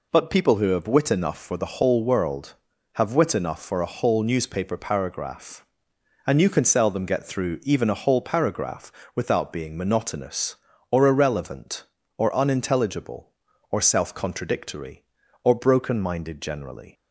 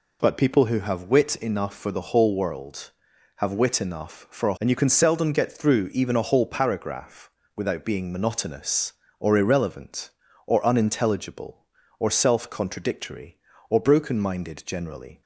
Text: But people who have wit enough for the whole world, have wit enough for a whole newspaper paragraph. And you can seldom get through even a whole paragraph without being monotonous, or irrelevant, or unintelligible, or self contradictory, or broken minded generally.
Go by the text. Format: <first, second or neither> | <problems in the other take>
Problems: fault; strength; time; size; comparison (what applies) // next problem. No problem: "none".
first | skips "whole newspaper paragraph"; at 4.5 s // pauses between "paragraph" and "without"; slight; at 7.2 s; 0.26 s long; slight in the first